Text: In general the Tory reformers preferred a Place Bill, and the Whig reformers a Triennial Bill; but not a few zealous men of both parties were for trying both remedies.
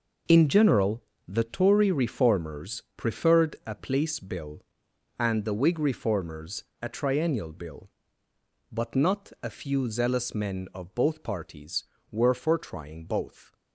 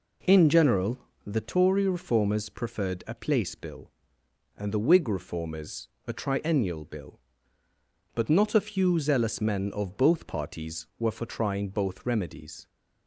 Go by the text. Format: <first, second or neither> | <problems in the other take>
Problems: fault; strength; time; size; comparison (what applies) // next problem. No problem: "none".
second | pauses between "general" and "the"; slight; at 1.0 s; 0.24 s long; slight in the second // pauses between "reformers" and "a"; slight; at 6.6 s; 0.16 s long; slight in the second // stops before "remedies"; at 13.5 s